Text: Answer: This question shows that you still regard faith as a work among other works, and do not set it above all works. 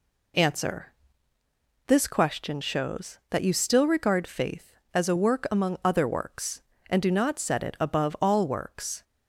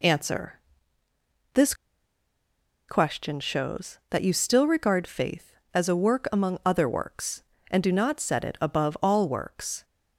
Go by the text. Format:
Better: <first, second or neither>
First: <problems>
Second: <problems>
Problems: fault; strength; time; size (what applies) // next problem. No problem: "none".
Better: first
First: none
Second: pauses between "This" and "question"; at 1.7 s; 1.1 s long